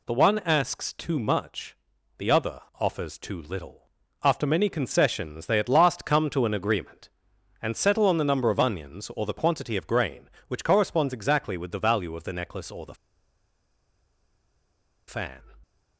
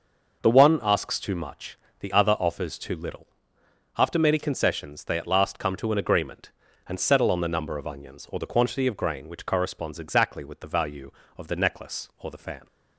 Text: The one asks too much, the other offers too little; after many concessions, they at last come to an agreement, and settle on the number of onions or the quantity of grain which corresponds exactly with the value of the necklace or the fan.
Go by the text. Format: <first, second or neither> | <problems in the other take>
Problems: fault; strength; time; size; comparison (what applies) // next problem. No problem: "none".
second | pauses between "other" and "offers"; slight; at 2.5 s; 0.18 s long // pauses between "the" and "fan"; strong; at 12.9 s; 2.1 s long